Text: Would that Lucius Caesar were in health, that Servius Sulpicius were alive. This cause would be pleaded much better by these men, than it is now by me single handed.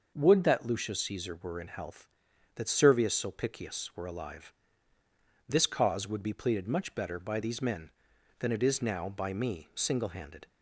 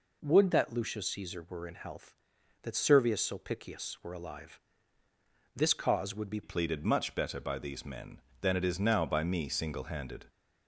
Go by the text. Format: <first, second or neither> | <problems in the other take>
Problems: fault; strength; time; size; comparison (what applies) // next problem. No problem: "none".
first | changes voice at "pleaded"; from 6.4 s on; 3.8 s long